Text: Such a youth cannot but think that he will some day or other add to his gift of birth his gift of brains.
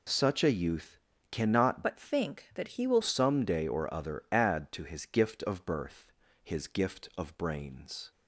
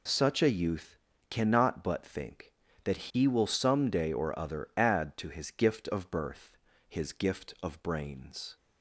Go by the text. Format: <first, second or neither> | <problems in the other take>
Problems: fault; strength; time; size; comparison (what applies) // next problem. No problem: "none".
second | pauses between "youth" and "cannot"; slight; at 0.9 s; 0.34 s long; slight in the second // changes voice from "but" to "will"; from 1.8 to 3.0 s; 1.2 s long // pauses between "birth" and "his"; at 6.0 s; 0.38 s long; also in the second